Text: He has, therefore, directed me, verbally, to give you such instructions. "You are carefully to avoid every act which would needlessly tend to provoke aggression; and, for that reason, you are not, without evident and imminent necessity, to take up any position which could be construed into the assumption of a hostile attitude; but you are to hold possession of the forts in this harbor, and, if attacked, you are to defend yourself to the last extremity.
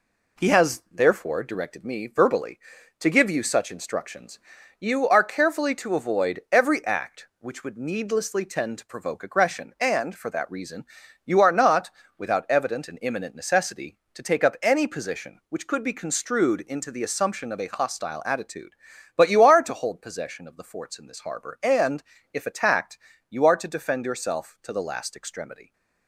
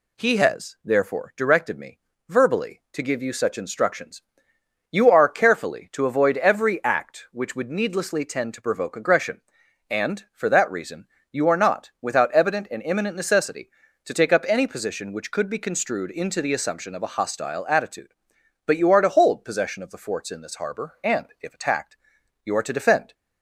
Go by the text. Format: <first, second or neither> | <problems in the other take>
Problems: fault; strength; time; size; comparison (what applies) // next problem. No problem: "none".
first | stops before "yourself to the last extremity"; at 23.1 s